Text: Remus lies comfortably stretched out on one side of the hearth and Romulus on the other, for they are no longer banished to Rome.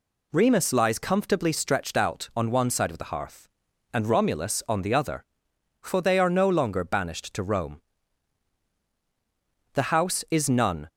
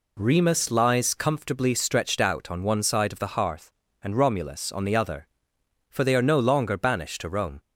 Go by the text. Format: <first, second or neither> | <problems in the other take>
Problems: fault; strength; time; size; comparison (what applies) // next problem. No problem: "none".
second | goes on to say "The house is none"; noticeable; from 9.7 s on; 1.1 s long